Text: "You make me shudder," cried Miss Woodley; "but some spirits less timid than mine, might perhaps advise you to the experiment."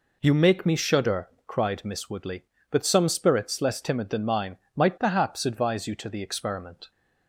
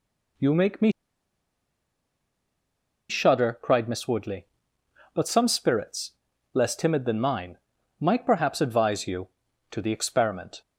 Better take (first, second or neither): first